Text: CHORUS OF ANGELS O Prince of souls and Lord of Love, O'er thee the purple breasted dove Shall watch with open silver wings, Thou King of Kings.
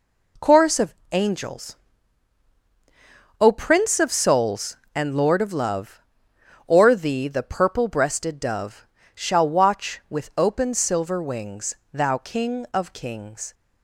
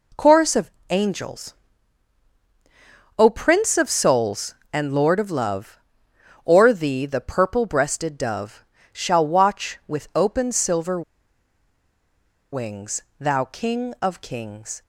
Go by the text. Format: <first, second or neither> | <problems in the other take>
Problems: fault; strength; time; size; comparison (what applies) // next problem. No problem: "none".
first | pauses between "OF" and "ANGELS"; slight; at 0.7 s; 0.20 s long; slight in the first // pauses between "ANGELS" and "O"; strong; at 1.5 s; 1.6 s long; strong in the first // pauses between "dove" and "Shall"; slight; at 8.6 s; 0.30 s long; slight in the first // pauses between "silver" and "wings"; strong; at 11.0 s; 1.5 s long